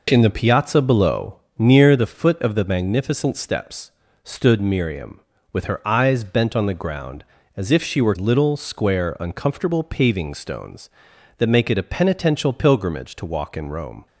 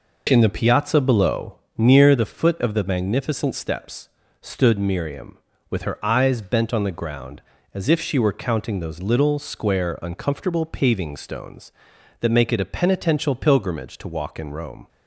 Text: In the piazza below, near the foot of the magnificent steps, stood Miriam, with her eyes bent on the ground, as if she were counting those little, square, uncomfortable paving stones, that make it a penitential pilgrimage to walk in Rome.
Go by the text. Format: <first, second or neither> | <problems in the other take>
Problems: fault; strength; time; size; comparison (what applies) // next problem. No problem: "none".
second | skips "counting those"; at 8.1 s